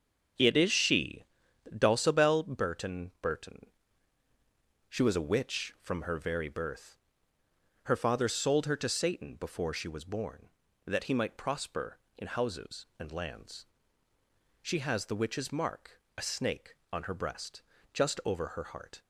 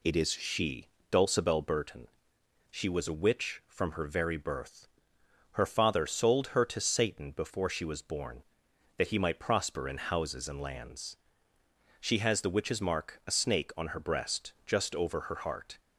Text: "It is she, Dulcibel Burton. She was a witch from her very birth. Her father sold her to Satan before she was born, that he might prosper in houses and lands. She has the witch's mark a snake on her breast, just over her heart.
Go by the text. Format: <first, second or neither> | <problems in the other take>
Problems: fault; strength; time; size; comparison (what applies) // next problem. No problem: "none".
second | starts louder than the rest; until 1.8 s; 6.5 dB // says "Burton" twice; at 3.2 s // pauses between "mark" and "a"; slight; at 16.0 s; 0.16 s long